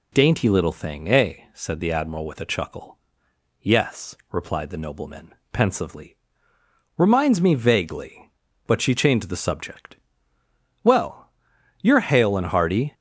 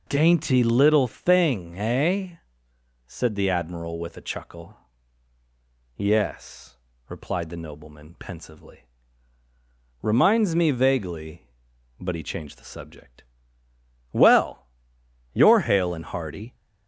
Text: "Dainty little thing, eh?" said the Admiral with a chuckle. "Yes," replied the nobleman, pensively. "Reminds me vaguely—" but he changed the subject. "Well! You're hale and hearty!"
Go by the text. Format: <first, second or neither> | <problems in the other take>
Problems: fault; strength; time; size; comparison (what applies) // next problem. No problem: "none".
second | says "she" for "he"; at 8.7 s